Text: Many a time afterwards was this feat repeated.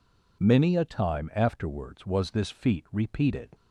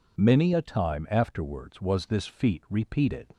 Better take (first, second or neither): neither